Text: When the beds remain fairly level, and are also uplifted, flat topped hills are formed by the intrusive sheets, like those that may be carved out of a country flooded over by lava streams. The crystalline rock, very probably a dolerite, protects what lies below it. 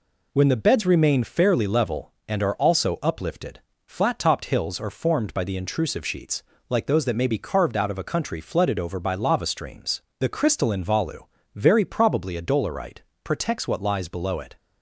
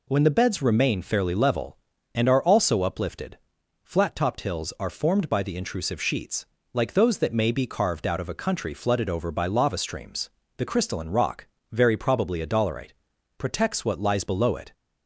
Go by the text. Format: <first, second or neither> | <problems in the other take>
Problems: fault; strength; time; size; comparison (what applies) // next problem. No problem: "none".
second | says "volu" for "rock"; at 10.8 s